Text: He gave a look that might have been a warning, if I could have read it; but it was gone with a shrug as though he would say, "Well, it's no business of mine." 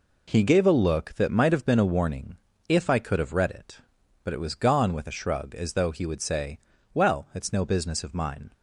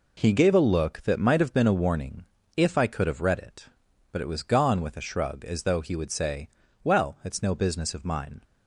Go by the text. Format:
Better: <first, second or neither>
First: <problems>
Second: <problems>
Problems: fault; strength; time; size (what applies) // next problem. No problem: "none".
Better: neither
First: none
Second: none